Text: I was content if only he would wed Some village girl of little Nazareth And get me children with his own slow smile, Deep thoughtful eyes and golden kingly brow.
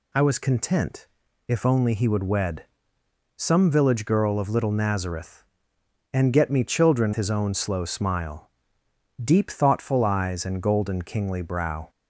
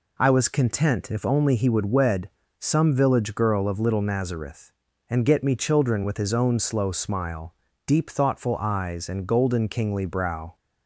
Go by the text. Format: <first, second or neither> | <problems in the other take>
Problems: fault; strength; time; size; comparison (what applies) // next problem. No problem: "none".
second | pauses between "content" and "if"; at 1.0 s; 0.42 s long // pauses between "wed" and "Some"; noticeable; at 2.6 s; 0.70 s long; slight in the second // skips "with"; at 7.1 s